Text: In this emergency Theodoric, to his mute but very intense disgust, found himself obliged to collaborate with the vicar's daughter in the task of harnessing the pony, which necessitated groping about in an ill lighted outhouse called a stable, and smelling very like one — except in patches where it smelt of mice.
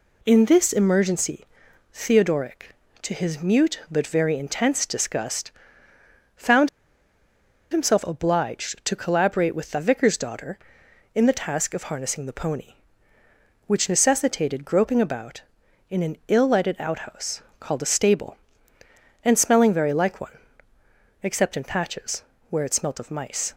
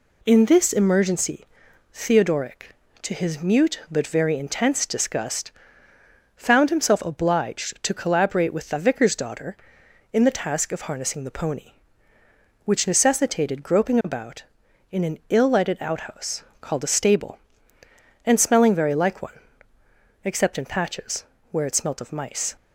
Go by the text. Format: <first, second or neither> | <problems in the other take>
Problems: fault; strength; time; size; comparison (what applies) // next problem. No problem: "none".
second | pauses between "emergency" and "Theodoric"; noticeable; at 1.4 s; 0.48 s long; noticeable in the second // pauses between "found" and "himself"; at 6.6 s; 1.0 s long // pauses between "outhouse" and "called"; slight; at 17.4 s; 0.18 s long; slight in the second // pauses between "patches" and "where"; slight; at 22.2 s; 0.28 s long; slight in the second